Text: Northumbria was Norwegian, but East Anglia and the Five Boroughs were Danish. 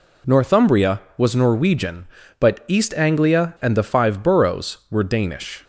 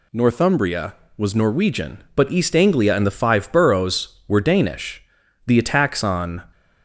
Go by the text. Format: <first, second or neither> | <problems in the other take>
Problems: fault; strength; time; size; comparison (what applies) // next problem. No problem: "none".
first | goes on to say "The attacks on"; noticeable; from 5.4 s on; 1.0 s long